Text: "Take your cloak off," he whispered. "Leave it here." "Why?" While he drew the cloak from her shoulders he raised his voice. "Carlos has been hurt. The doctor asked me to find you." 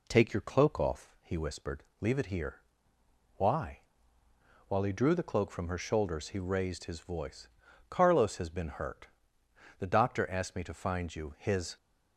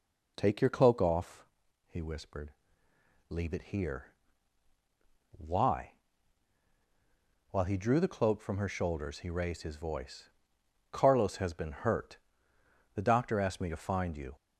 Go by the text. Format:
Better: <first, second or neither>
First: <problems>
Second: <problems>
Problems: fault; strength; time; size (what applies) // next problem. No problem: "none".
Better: second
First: goes on to say "His"; slight; from 11.3 s on; 0.38 s long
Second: none